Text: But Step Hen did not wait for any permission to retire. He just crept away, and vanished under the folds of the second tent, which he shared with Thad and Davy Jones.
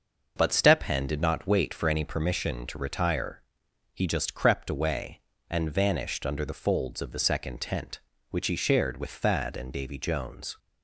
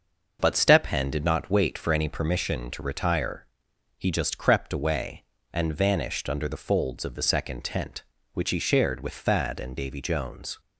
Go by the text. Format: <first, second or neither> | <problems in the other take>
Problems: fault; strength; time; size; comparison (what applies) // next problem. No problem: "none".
neither | starts louder than the rest; noticeable; the same in both